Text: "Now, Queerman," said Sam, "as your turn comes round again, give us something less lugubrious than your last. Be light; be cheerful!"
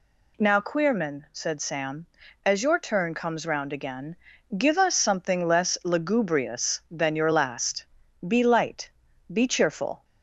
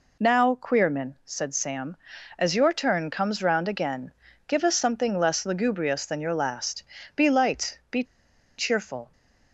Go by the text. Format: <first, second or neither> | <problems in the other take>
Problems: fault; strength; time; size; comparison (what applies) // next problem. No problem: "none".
first | pauses between "be" and "cheerful"; noticeable; at 8.0 s; 0.54 s long